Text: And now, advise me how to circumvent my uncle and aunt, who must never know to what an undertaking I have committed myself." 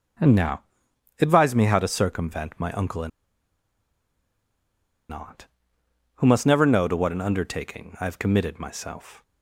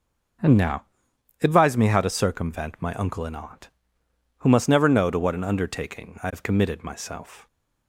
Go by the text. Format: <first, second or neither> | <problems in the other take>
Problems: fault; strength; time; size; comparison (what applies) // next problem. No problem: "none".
second | starts louder than the rest; until 1.7 s; 6.5 dB // pauses between "and" and "aunt"; strong; at 3.0 s; 2.0 s long